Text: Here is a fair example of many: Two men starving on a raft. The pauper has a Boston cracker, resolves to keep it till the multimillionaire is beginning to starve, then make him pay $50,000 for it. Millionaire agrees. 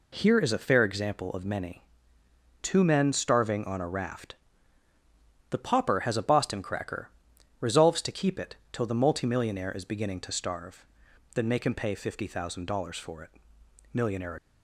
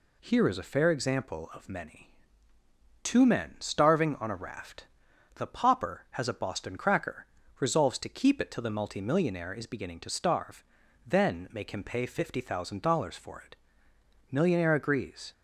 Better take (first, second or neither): second